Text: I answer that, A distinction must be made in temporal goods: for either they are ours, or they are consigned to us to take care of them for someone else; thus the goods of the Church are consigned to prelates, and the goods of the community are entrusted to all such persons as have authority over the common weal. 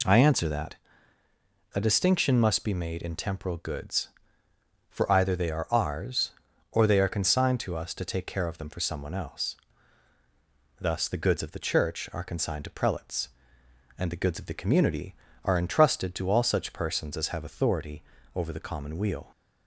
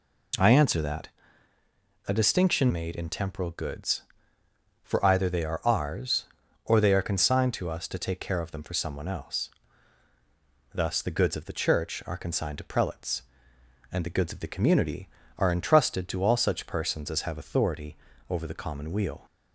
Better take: first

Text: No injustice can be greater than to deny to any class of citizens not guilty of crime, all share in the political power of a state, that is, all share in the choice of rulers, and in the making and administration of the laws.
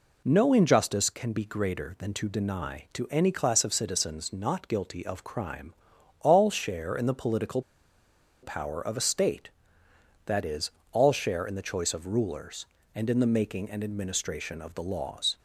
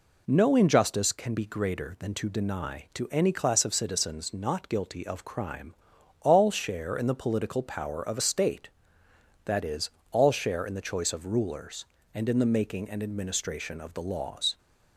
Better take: second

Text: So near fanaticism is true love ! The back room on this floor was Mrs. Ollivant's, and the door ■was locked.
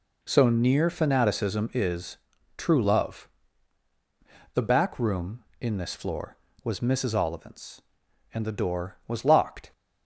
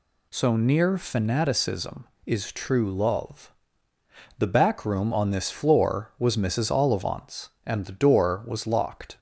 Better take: second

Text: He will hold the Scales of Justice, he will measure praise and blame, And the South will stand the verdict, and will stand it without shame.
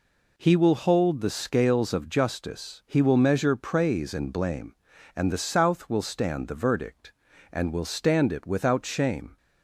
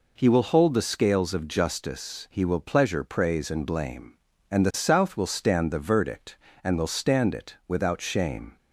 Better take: first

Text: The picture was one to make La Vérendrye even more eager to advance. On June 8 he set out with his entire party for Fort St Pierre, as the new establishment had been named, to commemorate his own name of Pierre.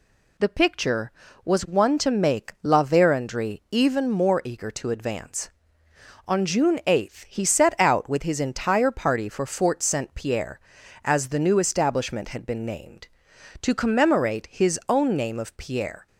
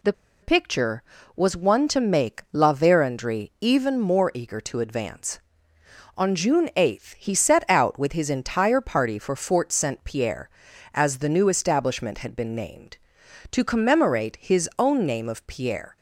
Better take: first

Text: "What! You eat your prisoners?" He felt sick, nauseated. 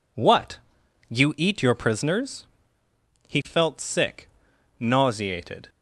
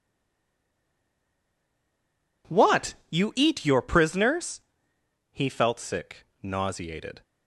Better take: first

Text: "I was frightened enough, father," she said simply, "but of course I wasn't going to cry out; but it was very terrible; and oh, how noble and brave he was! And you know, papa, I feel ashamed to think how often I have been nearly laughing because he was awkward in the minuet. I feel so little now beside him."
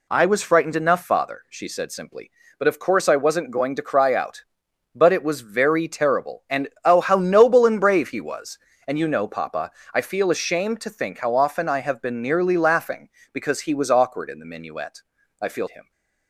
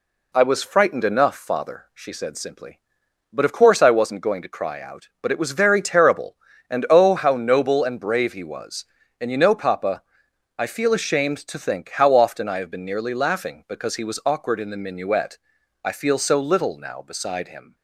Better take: second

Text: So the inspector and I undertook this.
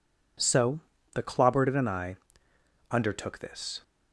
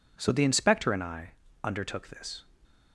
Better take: second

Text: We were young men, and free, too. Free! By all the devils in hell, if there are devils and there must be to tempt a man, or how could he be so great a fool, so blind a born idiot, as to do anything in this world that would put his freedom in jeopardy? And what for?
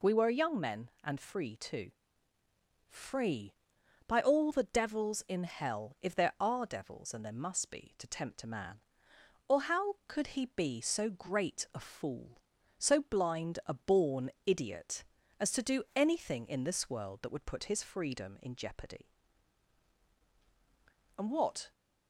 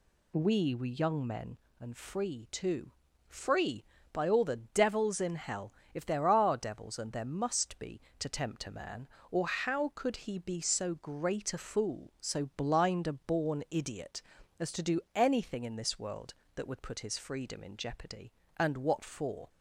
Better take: second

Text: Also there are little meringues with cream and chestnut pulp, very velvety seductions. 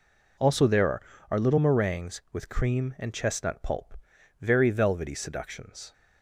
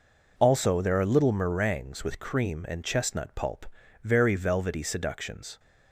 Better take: second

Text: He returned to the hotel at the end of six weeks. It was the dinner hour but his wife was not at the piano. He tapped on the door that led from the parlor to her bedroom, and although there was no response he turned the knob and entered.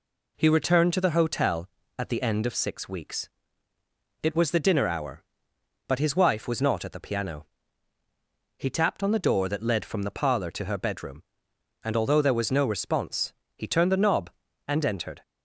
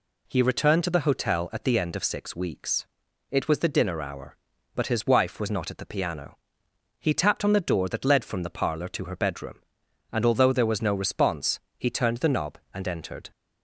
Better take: neither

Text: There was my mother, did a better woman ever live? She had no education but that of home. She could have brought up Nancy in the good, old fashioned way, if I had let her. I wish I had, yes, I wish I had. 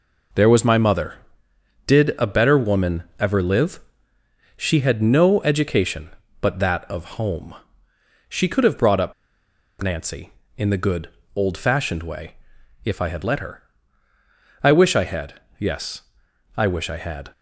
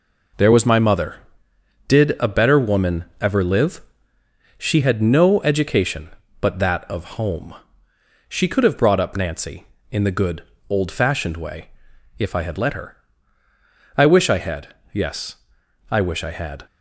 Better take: second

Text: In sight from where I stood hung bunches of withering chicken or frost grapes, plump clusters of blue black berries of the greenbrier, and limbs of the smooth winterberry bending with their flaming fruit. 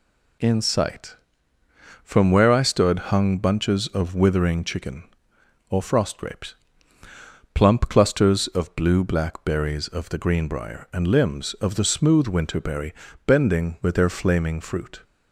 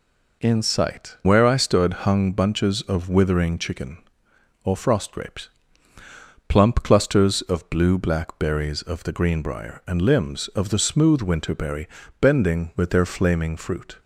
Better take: first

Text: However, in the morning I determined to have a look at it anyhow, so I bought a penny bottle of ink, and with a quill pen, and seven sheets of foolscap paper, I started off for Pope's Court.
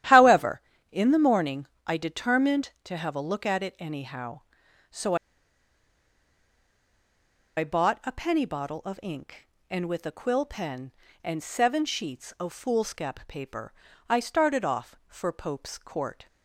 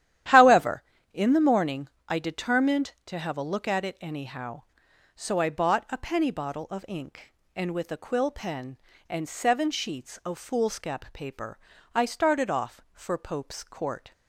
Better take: second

